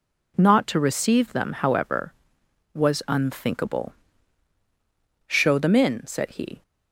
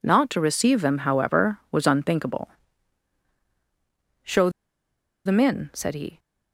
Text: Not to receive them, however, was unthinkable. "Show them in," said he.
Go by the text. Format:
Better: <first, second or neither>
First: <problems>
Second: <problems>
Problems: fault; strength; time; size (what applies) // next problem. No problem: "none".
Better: first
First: none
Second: pauses between "Show" and "them"; noticeable; at 4.4 s; 0.76 s long